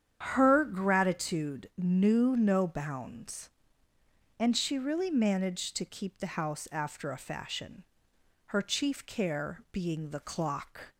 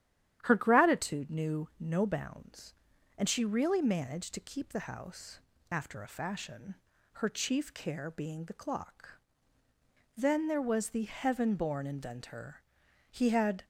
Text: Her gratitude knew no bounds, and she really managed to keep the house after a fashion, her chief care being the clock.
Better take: first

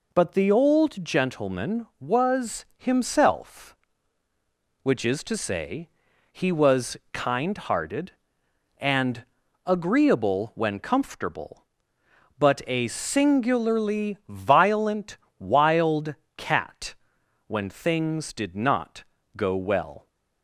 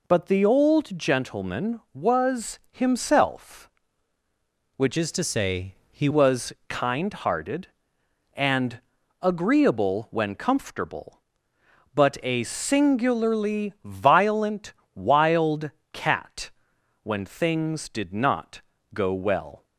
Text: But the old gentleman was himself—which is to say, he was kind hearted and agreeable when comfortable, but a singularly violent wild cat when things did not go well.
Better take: first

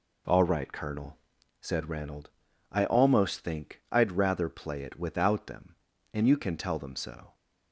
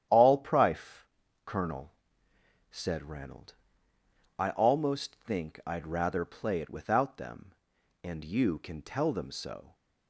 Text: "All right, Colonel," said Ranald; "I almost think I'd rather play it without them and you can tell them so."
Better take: first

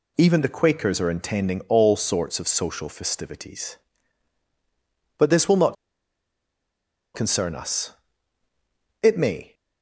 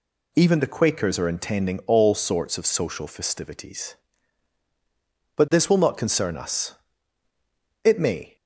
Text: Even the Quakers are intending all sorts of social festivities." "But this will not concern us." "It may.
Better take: second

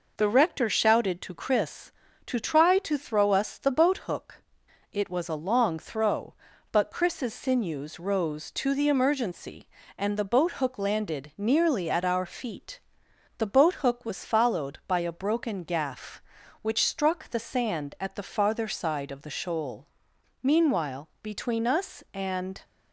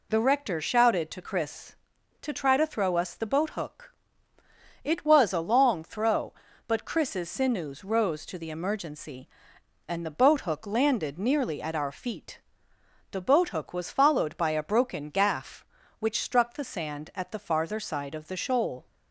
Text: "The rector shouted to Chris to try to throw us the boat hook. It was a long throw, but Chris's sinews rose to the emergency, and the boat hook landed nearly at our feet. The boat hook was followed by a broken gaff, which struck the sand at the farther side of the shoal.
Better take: second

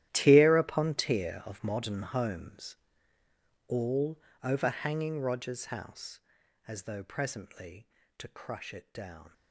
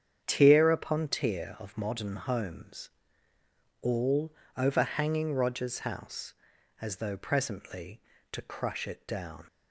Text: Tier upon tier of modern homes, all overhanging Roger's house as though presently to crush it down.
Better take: second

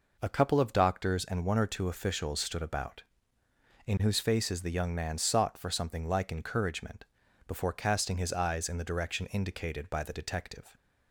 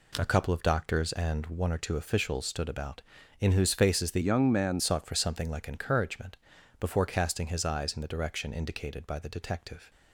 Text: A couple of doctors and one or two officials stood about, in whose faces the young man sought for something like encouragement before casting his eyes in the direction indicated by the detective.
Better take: first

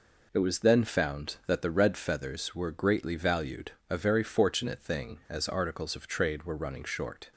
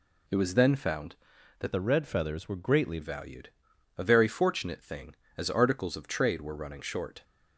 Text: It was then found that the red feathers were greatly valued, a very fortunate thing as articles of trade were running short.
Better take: first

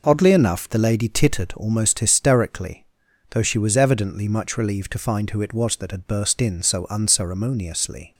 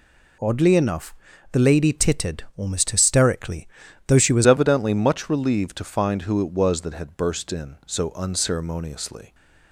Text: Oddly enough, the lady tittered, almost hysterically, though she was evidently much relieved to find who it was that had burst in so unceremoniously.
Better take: first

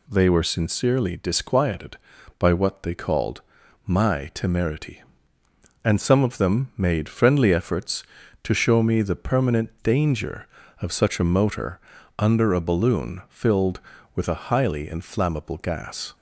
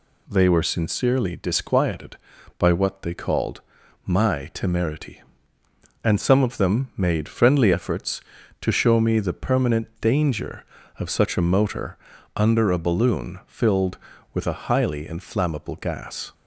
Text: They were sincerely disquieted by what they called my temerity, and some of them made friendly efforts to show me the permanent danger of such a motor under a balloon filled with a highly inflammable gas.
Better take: neither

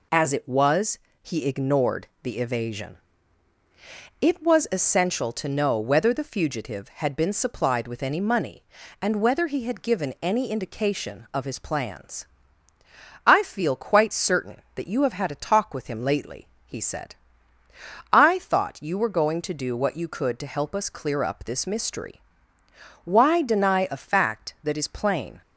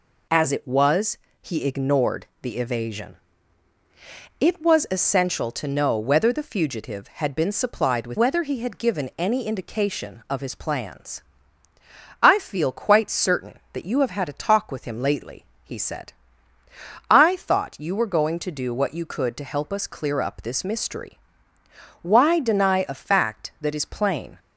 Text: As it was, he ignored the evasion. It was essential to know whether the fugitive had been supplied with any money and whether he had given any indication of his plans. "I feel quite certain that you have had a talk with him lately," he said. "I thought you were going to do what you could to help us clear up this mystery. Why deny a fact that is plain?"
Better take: first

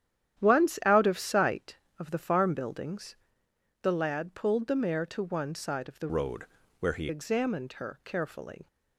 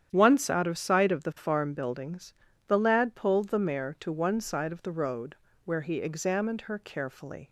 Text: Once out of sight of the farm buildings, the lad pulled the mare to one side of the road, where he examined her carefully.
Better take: second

